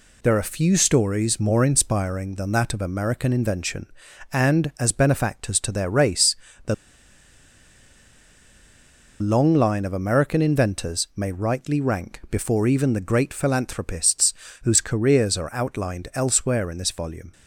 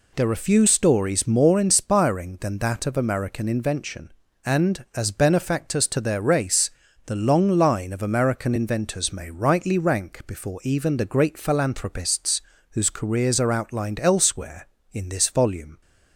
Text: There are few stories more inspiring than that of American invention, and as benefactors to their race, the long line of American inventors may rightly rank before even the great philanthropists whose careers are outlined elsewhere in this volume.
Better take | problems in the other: second | pauses between "the" and "long"; strong; at 6.7 s; 2.4 s long // pauses between "philanthropists" and "whose"; slight; at 14.3 s; 0.30 s long; slight in the second

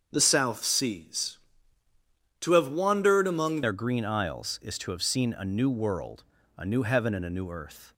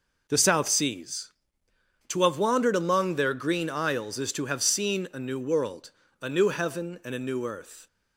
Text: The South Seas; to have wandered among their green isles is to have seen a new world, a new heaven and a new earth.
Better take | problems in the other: second | starts louder than the rest; until 1.1 s; 6.5 dB // changes voice at "their"; from 3.6 s on; 4.3 s long

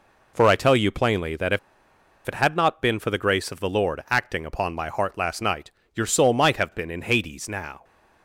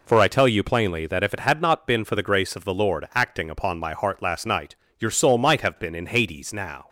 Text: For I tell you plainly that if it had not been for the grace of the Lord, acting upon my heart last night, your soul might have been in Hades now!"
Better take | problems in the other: second | pauses between "if" and "it"; noticeable; at 1.5 s; 0.68 s long

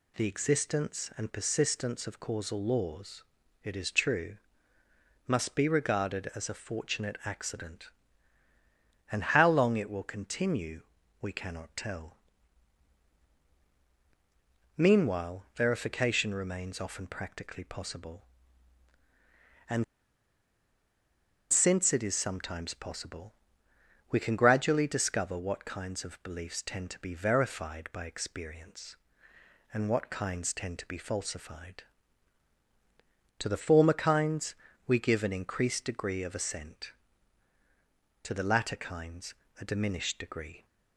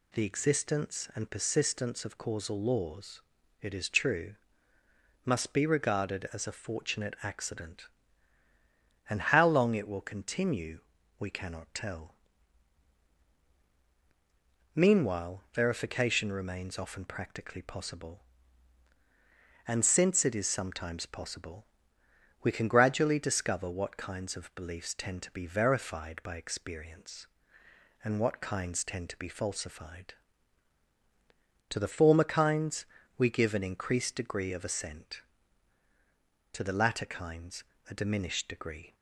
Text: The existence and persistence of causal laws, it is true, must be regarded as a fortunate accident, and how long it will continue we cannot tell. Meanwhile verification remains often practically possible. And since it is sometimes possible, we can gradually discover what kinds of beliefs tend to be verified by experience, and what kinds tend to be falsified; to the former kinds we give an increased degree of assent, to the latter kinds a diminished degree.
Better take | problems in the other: second | pauses between "continue" and "we"; at 10.8 s; 0.38 s long; also in the second // pauses between "And" and "since"; strong; at 19.8 s; 1.6 s long // pauses between "kinds" and "we"; slight; at 34.5 s; 0.34 s long; slight in the second // pauses between "kinds" and "a"; slight; at 39.3 s; 0.28 s long; slight in the second

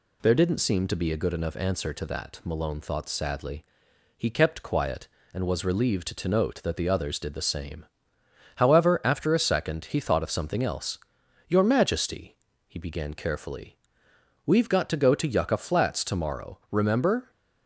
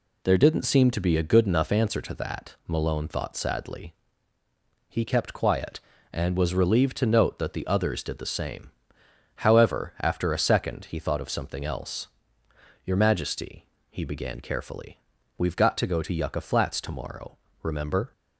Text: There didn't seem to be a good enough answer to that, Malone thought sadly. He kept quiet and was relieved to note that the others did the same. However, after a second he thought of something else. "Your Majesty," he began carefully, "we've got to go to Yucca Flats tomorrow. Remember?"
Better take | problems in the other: neither | none

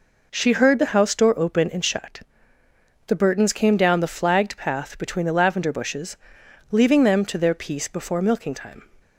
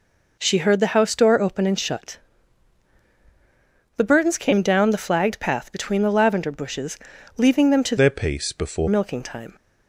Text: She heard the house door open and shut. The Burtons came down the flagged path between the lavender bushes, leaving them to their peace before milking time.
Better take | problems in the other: first | changes voice from "their" to "before"; from 7.9 to 8.8 s; 0.9 s long

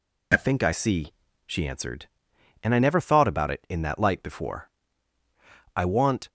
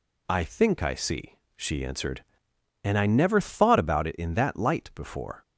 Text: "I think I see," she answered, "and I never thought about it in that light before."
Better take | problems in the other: second | goes on to say "I want"; from 5.7 s on; 0.54 s long

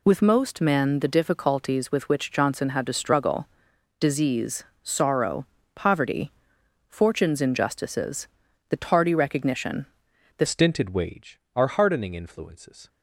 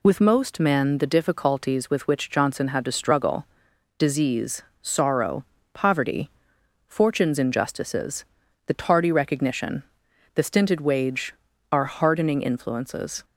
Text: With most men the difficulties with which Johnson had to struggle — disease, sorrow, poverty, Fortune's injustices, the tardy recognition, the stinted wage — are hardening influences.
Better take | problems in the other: second | changes voice at "stinted"; from 10.4 s on; 2.4 s long

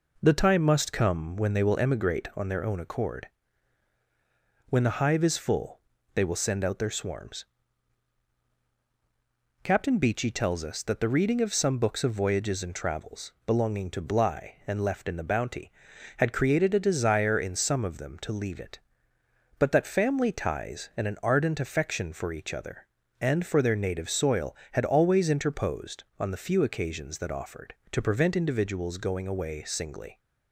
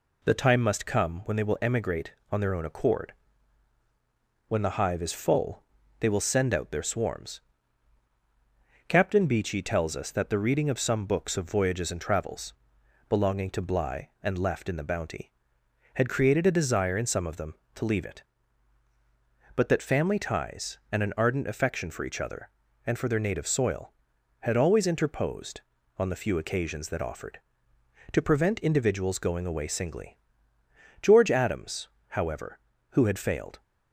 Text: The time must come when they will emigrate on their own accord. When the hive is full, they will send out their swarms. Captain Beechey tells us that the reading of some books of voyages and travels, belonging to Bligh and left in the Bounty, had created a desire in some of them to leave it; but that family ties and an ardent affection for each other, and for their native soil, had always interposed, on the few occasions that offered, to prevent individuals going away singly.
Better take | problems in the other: first | goes on to say "George Adams however who had failed"; strong; from 30.9 s on; 2.6 s long

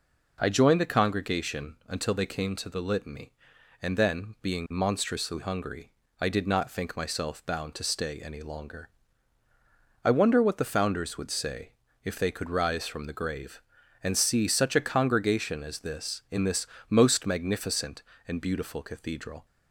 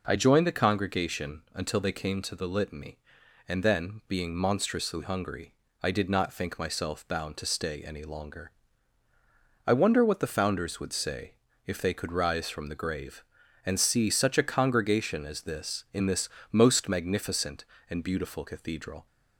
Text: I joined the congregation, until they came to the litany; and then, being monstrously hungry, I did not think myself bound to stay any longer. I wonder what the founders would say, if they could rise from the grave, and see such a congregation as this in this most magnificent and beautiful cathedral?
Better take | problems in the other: neither | pauses between "this" and "most"; slight; the same in both

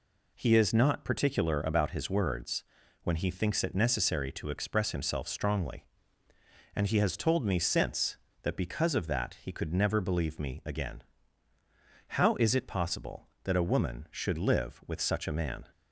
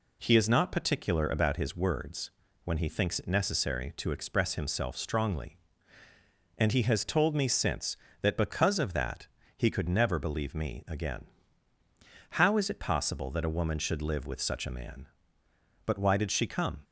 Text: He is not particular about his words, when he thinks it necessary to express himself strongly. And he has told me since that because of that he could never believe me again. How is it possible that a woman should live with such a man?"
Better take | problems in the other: first | pauses between "that" and "he"; slight; at 9.2 s; 0.26 s long // goes on to say "But why did she come"; noticeable; from 15.8 s on; 0.96 s long

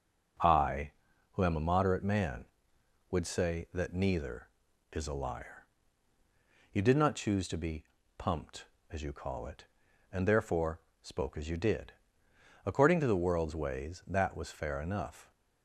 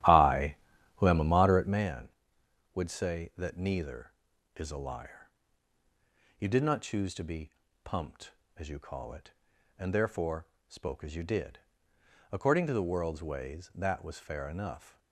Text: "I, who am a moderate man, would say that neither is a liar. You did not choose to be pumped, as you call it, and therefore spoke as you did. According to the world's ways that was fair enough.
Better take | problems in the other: first | starts louder than the rest; strong; until 1.9 s; 12.5 dB // pauses between "be" and "pumped"; slight; at 7.5 s; 0.34 s long; slight in the first // pauses between "therefore" and "spoke"; slight; at 10.4 s; 0.22 s long; slight in the first

